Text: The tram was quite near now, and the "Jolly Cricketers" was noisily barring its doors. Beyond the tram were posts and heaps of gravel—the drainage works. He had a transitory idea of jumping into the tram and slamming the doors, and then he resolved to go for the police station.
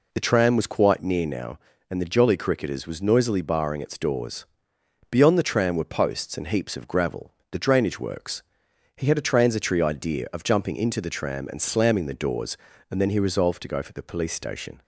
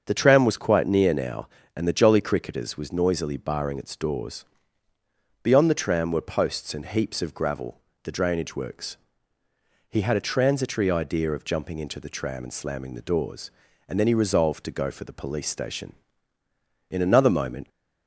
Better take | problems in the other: first | starts louder than the rest; until 1.0 s; 7 dB // goes on to say "In another moment"; noticeable; from 16.9 s on; 0.78 s long

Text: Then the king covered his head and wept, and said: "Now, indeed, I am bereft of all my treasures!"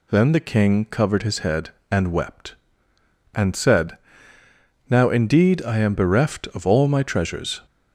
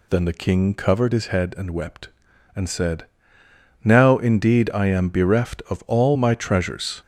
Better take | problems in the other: neither | none

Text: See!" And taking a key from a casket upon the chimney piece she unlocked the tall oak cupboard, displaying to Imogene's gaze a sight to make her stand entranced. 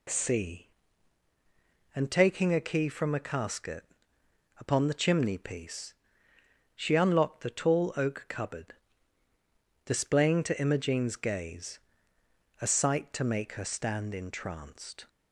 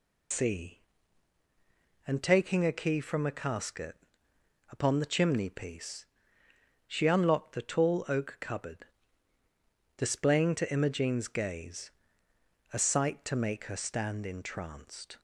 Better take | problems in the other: first | loses the start of "See"; at 0.3 s; 120 ms // pauses between "casket" and "upon"; noticeable; at 3.9 s; 0.74 s long; noticeable in the first // pauses between "piece" and "she"; noticeable; at 6.0 s; 0.82 s long; noticeable in the first // pauses between "gaze" and "a"; noticeable; at 11.9 s; 0.80 s long; noticeable in the first

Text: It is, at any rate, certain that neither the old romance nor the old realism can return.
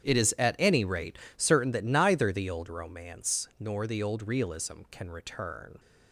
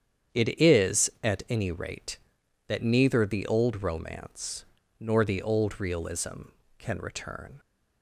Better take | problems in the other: first | starts louder than the rest; strong; until 1.5 s; 8.5 dB; strong in the first // skips "certain"; at 2.4 s // pauses between "romance" and "nor"; slight; at 4.6 s; 0.36 s long

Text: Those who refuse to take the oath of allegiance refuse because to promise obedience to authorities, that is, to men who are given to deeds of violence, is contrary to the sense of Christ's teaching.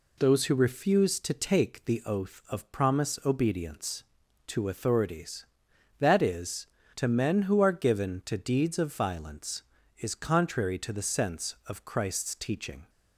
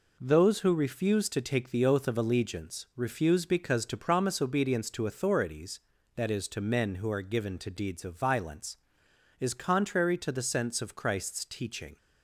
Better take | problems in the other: second | skips "allegiance refuse because to"; at 2.7 s

